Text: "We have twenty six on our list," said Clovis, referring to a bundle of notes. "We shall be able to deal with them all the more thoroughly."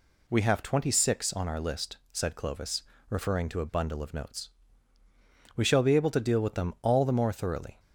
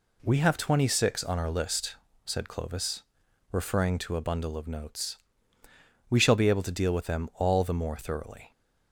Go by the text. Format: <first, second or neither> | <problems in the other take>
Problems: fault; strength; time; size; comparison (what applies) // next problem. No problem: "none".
neither | none